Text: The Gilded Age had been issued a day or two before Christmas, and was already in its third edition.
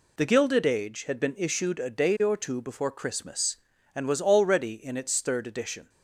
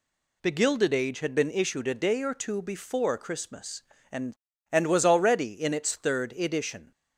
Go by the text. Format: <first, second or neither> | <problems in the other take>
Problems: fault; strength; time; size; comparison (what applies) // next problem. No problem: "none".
first | says "and" twice; at 4.7 s